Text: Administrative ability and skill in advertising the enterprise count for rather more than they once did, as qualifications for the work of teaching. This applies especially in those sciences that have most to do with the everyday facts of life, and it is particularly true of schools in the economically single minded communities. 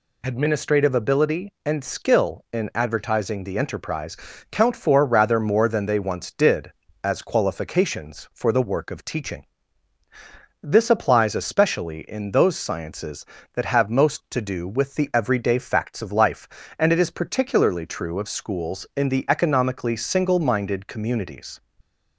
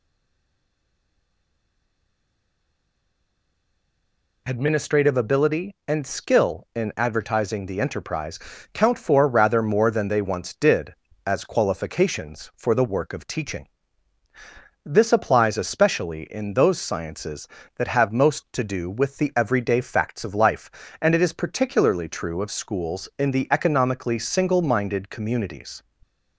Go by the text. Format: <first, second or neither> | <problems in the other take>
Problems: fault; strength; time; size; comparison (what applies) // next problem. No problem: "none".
first | stays silent before the first word; strong; until 4.4 s; 4.4 s long // pauses between "enterprise" and "count"; slight; at 8.3 s; 0.36 s long; slight in the first